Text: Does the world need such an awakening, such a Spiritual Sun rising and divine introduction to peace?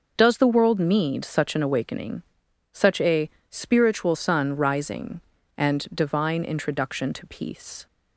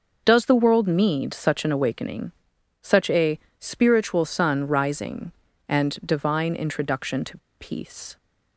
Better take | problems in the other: first | pauses between "a" and "Spiritual"; slight; at 3.3 s; 0.20 s long; slight in the first // pauses between "to" and "peace"; slight; at 7.3 s; 0.22 s long

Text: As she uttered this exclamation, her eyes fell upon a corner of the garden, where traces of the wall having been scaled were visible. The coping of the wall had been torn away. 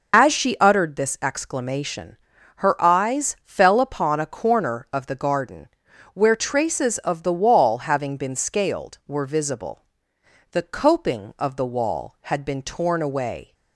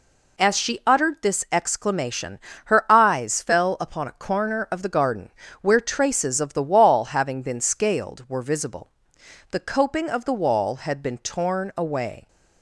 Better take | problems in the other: second | loses the start of "As"; at 0.1 s; 75 ms

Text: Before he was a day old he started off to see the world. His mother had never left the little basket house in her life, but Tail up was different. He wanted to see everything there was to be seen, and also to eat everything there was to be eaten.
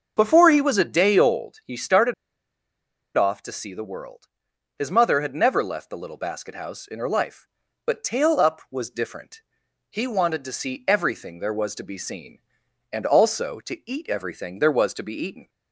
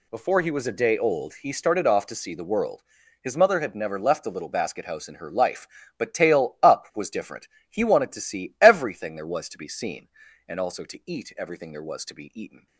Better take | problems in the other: second | starts louder than the rest; until 1.1 s; 6.5 dB // pauses between "started" and "off"; at 2.1 s; 1.0 s long

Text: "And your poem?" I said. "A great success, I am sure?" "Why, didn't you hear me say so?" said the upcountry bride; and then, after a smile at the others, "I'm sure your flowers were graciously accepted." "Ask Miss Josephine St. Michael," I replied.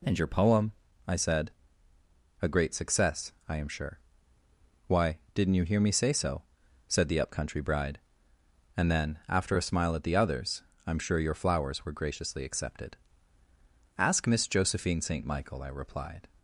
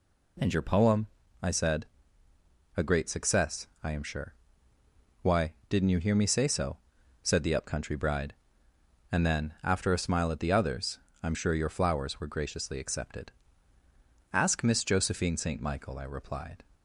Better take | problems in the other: neither | none

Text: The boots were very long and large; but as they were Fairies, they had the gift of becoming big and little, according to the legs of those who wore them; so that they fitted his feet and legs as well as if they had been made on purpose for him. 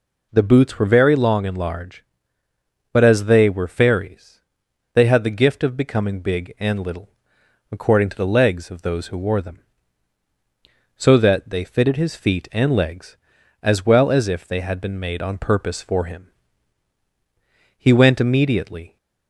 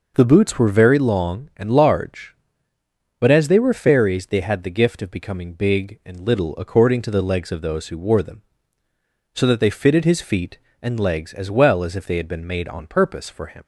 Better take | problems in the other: second | goes on to say "He went immediately"; noticeable; from 17.7 s on; 1.2 s long

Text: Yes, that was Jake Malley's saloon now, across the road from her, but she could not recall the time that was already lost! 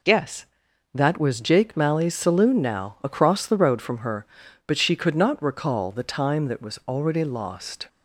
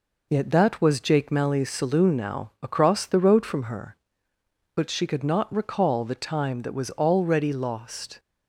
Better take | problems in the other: first | says "Yet" for "Yes"; at 0.2 s

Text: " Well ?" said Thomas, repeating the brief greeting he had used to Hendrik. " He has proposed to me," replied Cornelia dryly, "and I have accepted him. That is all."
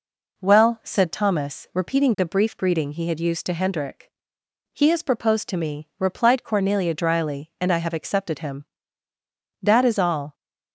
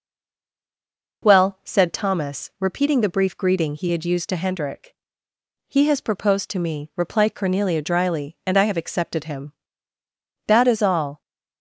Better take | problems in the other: first | stays silent before the first word; noticeable; until 1.2 s; 1.2 s long

